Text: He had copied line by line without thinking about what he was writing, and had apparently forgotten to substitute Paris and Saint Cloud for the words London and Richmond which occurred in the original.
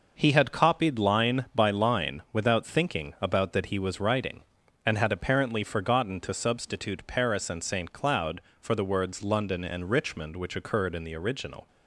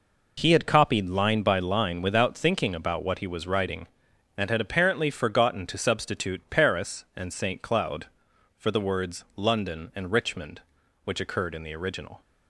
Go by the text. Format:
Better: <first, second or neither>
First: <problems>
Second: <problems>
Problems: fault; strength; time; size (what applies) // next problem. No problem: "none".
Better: second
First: says "that" for "what"; at 3.5 s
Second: none